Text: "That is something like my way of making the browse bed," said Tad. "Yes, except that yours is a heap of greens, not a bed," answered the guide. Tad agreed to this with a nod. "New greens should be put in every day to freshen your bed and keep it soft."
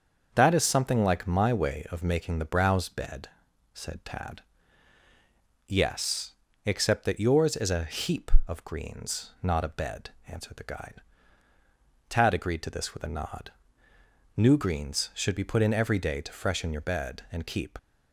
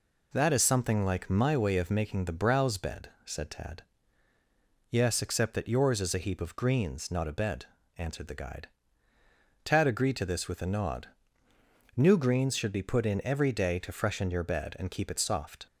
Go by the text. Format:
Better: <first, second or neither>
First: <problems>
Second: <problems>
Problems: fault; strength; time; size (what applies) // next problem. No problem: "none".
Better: second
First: starts louder than the rest; until 1.3 s; 6.5 dB // stops before "it soft"; at 17.7 s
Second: none